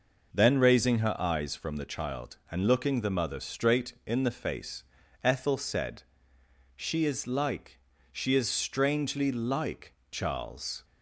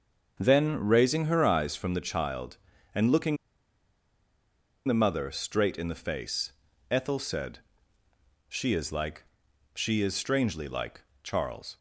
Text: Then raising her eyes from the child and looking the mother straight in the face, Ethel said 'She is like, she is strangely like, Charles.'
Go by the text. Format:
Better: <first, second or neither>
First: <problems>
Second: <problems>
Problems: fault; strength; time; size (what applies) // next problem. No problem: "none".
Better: first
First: pauses between "said" and "She"; noticeable; at 6.0 s; 0.74 s long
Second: starts louder than the rest; until 1.3 s; 6.5 dB // pauses between "looking" and "the"; strong; at 3.3 s; 1.5 s long // pauses between "said" and "She"; noticeable; at 7.5 s; 0.90 s long